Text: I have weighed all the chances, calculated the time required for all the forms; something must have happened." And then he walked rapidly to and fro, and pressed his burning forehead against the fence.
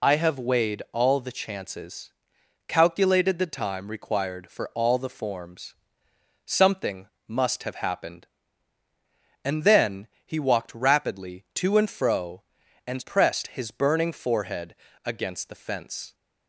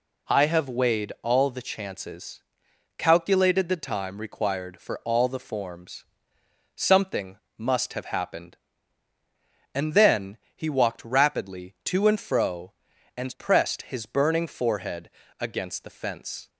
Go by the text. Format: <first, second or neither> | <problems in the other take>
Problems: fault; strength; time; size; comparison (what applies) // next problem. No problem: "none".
second | loses the start of "I"; at 0.0 s; 50 ms // pauses between "something" and "must"; slight; at 7.0 s; 0.20 s long; slight in the second // pauses between "then" and "he"; slight; at 10.0 s; 0.18 s long; slight in the second // pauses between "forehead" and "against"; slight; at 14.7 s; 0.32 s long; slight in the second